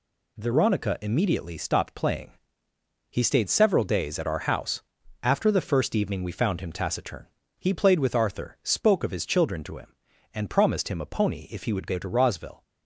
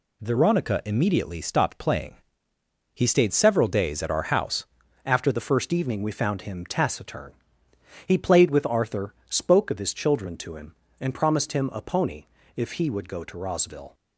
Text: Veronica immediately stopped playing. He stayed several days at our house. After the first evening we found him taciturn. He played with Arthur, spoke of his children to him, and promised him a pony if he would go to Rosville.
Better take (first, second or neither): first